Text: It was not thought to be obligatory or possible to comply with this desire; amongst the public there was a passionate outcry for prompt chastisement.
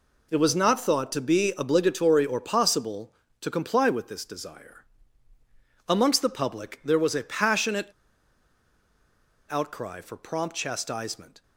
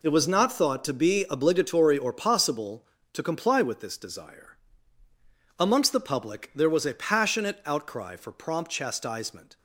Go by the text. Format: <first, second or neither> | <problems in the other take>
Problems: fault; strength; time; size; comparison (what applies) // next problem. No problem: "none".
second | pauses between "passionate" and "outcry"; strong; at 7.9 s; 1.5 s long